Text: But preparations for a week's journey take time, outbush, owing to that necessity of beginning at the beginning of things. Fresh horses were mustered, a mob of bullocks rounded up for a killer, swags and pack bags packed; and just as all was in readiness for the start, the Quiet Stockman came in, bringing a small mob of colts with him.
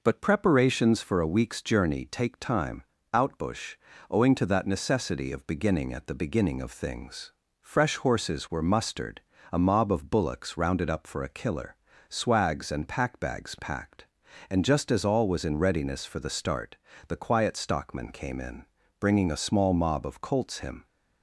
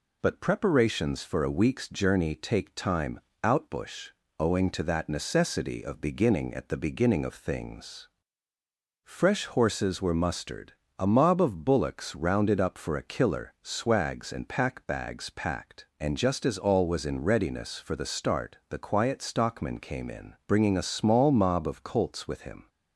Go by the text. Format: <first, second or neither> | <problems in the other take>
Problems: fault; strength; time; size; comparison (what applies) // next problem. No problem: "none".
second | skips "with"; at 20.5 s